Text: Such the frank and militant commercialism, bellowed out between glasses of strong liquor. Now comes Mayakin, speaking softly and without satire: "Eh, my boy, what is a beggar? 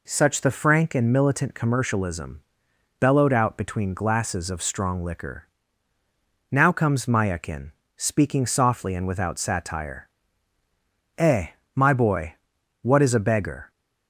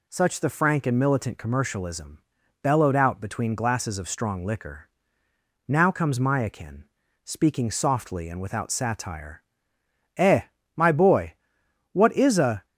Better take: first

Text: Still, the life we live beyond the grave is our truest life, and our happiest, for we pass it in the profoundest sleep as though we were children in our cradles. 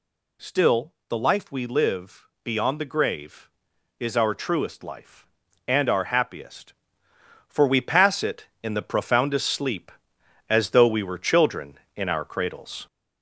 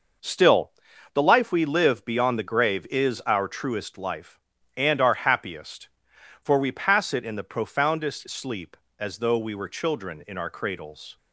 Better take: second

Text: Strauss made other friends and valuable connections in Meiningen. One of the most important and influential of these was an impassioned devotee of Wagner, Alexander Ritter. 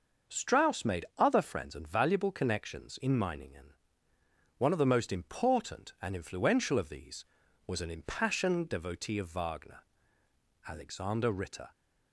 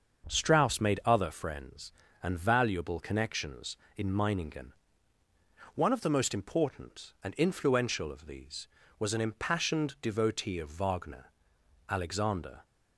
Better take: first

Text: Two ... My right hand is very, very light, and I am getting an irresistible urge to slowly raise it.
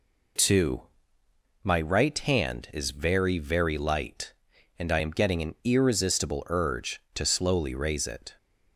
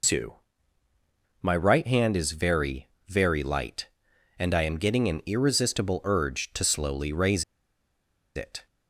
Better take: first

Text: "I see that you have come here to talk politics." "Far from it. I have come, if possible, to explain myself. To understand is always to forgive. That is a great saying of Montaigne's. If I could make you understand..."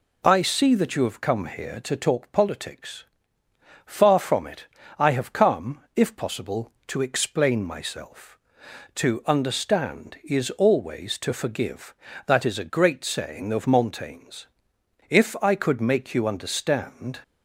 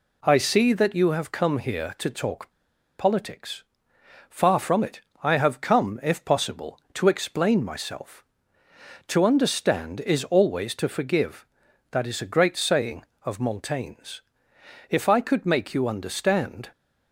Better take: first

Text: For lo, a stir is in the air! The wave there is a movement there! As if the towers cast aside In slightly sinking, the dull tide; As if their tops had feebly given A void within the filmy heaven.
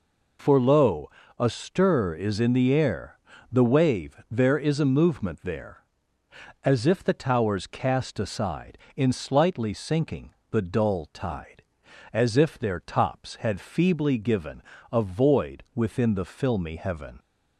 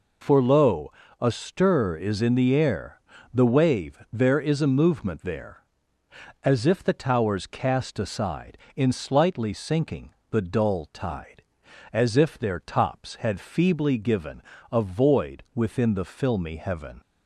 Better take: neither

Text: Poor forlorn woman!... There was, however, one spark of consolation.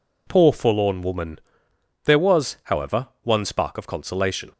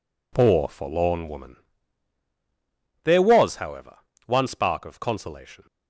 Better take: neither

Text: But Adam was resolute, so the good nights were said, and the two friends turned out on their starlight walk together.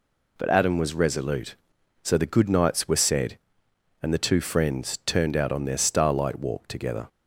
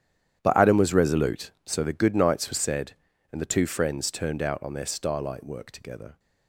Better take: first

